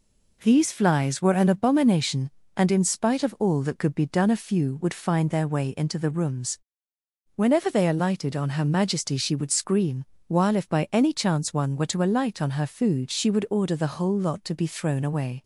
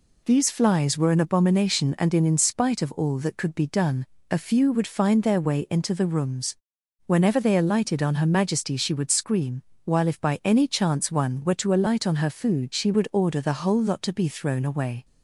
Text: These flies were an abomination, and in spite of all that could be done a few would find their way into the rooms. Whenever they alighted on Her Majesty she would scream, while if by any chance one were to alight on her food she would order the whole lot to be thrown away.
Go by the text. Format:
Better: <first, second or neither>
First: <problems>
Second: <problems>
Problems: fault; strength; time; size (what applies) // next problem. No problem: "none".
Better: first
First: none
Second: says "in" twice; at 2.2 s // pauses between "done" and "a"; slight; at 4.0 s; 0.26 s long